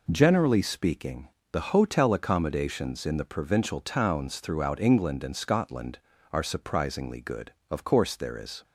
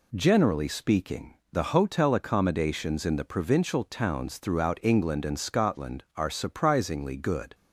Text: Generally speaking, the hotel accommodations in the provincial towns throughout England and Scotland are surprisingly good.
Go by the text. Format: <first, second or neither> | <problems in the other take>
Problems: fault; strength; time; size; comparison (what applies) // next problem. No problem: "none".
second | goes on to say "Of course there is"; noticeable; from 7.6 s on; 0.94 s long